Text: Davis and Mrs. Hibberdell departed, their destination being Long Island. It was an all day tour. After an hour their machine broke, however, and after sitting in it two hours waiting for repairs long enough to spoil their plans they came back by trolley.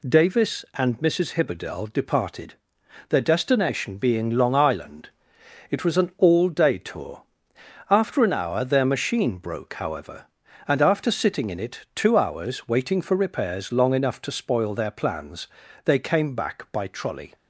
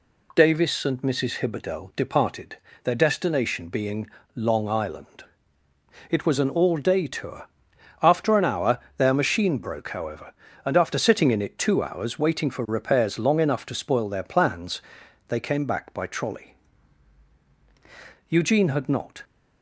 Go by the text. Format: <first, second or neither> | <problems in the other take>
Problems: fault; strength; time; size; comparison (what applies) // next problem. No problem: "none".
first | pauses between "being" and "Long"; slight; at 4.0 s; 0.26 s long // pauses between "hour" and "their"; slight; at 8.7 s; 0.16 s long // pauses between "plans" and "they"; noticeable; at 14.8 s; 0.46 s long; also in the first // goes on to say "Eugene had not"; noticeable; from 18.2 s on; 0.96 s long